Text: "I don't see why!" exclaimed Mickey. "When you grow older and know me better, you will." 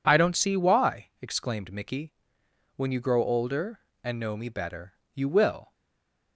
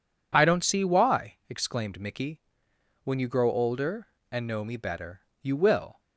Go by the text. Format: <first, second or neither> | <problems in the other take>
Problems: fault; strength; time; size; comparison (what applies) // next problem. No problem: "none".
second | stays silent after the last word; slight; from 5.7 s on; 0.6 s long